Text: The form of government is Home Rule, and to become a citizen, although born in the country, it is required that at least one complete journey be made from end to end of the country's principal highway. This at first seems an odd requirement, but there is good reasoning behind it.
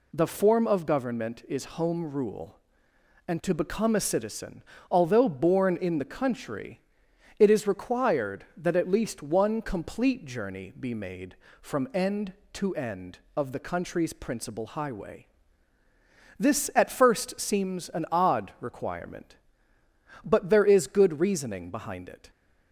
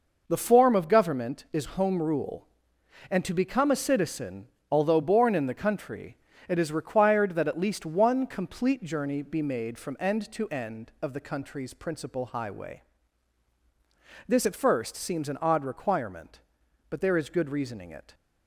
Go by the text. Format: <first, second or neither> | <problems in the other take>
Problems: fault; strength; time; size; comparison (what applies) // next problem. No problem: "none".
first | skips "behind"; at 17.8 s